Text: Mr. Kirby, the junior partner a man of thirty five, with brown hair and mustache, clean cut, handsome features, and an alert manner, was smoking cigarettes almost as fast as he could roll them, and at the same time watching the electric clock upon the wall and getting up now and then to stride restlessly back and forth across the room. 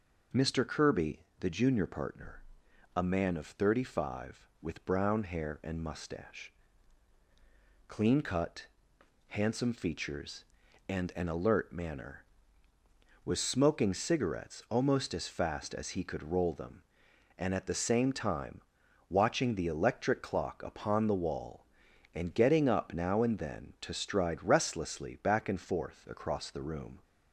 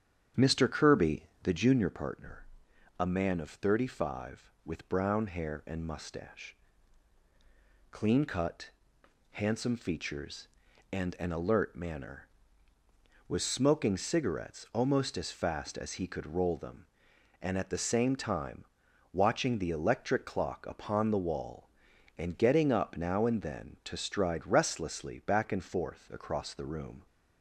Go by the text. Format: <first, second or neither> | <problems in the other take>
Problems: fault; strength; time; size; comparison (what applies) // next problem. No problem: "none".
first | starts louder than the rest; strong; until 1.9 s; 8.5 dB // pauses between "partner" and "a"; noticeable; at 2.4 s; 0.54 s long; noticeable in the first // pauses between "time" and "watching"; noticeable; at 18.6 s; 0.48 s long; noticeable in the first